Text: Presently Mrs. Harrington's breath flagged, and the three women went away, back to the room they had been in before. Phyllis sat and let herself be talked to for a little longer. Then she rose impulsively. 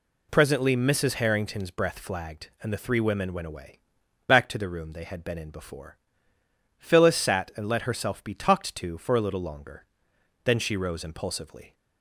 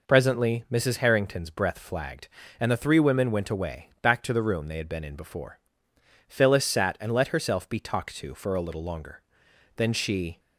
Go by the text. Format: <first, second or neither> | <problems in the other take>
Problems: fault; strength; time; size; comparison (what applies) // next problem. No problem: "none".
first | stops before "rose impulsively"; at 10.3 s